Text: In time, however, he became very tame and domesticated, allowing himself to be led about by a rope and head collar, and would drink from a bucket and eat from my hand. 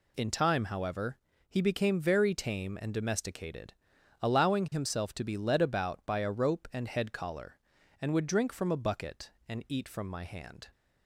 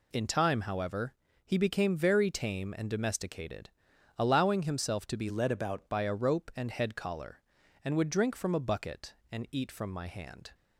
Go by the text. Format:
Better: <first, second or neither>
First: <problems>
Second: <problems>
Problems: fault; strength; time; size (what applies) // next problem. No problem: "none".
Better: first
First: none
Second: changes voice from "led" to "about"; from 5.2 to 5.8 s; 0.6 s long